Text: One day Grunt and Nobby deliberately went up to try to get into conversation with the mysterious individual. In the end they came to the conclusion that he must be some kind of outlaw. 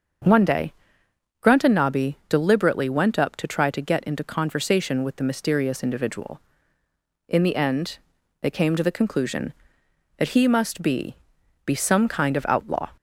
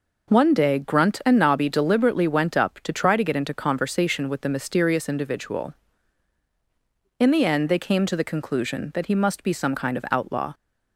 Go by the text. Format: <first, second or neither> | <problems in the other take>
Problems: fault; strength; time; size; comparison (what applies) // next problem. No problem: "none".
second | starts louder than the rest; until 1.9 s; 6.5 dB // pauses between "day" and "Grunt"; noticeable; at 0.7 s; 0.68 s long // pauses between "end" and "they"; at 7.9 s; 0.42 s long // says "be" twice; at 11.6 s